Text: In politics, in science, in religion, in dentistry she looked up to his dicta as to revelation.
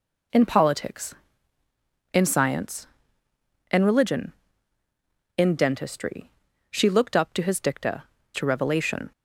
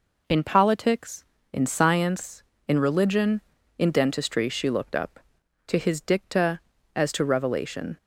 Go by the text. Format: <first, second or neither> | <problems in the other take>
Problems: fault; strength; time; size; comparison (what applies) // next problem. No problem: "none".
second | pauses between "dentistry" and "she"; at 6.3 s; 0.40 s long // skips "as"; at 8.1 s